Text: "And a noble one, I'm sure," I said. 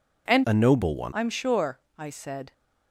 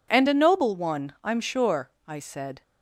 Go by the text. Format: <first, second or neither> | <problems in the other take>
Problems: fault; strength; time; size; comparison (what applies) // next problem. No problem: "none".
second | changes voice from "a" to "one"; from 0.4 to 1.1 s; 0.7 s long